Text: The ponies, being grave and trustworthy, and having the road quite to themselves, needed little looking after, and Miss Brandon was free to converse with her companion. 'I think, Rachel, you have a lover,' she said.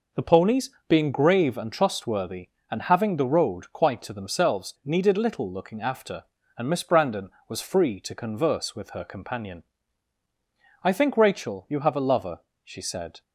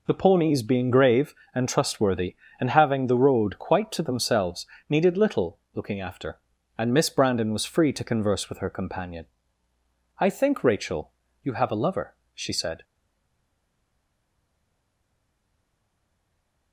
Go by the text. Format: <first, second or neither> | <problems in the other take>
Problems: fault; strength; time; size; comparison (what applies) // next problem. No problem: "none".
first | pauses between "little" and "looking"; slight; at 5.5 s; 0.16 s long // stays silent after the last word; strong; from 12.8 s on; 3.9 s long